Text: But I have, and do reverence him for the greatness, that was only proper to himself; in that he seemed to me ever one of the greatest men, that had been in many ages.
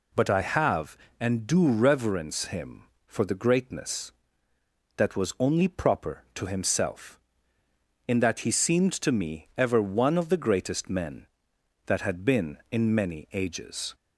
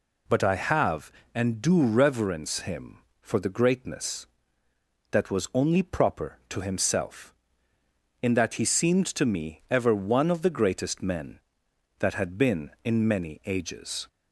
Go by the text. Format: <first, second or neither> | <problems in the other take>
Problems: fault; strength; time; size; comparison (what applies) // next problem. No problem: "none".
neither | none